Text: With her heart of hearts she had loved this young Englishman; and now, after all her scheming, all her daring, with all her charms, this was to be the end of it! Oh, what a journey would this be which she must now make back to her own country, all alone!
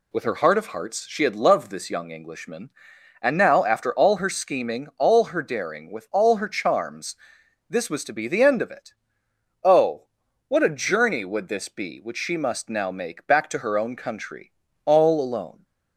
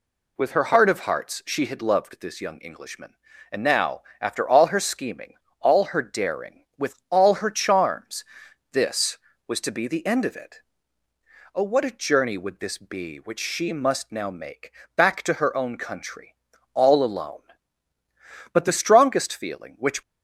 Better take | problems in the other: first | pauses between "make" and "back"; slight; at 14.7 s; 0.24 s long // goes on to say "But the strongest feeling which"; from 18.5 s on; 1.4 s long

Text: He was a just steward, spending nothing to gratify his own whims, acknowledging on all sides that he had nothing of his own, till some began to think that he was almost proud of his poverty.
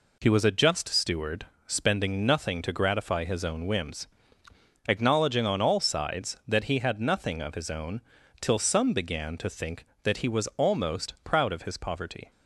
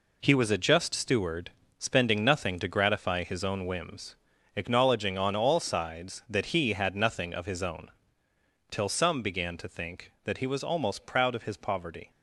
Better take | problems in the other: first | gets quieter; strong; throughout; 8 dB

